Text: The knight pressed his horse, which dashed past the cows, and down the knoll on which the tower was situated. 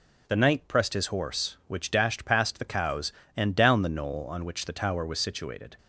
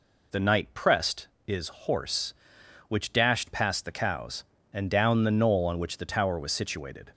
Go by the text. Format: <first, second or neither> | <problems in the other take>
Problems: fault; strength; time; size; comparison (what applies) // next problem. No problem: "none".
first | says "is" for "his"; at 1.4 s